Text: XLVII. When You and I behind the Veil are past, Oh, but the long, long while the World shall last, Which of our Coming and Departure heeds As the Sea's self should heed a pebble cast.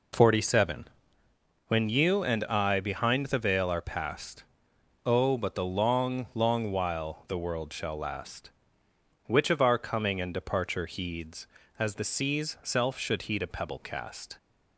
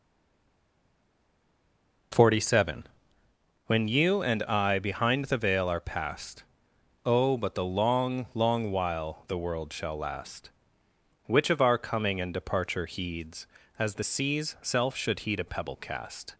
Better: first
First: none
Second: stays silent before the first word; noticeable; until 2.1 s; 2.1 s long

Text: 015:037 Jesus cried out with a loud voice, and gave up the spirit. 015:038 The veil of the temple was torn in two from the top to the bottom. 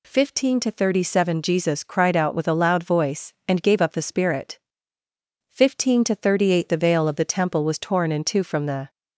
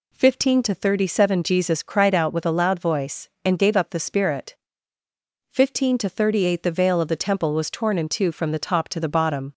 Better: second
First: stops before "top to the bottom"; at 8.8 s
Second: none

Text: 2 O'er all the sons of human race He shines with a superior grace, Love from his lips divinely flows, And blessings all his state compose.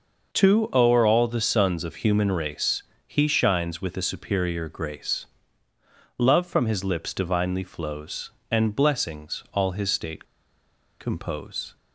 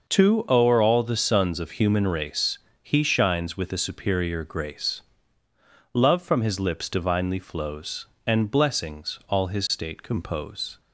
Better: second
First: pauses between "race" and "He"; slight; at 2.8 s; 0.22 s long // pauses between "state" and "compose"; noticeable; at 10.2 s; 0.76 s long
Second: pauses between "race" and "He"; slight; at 2.5 s; 0.22 s long

